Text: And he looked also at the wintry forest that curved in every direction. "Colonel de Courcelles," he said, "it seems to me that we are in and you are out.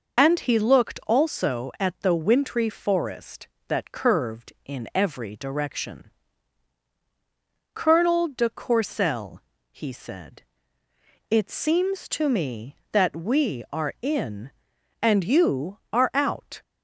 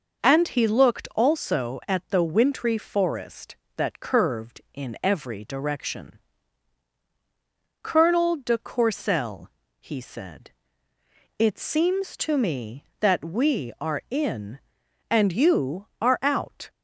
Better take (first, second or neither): second